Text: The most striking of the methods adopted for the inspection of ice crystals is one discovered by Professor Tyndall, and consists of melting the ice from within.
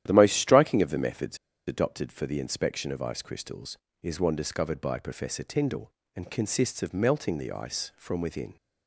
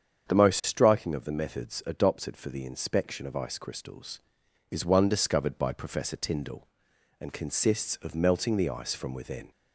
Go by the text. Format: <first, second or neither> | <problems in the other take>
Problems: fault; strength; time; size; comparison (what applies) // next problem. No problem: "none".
second | starts louder than the rest; strong; until 1.0 s; 11.5 dB; strong in the second // pauses between "methods" and "adopted"; slight; at 1.3 s; 0.30 s long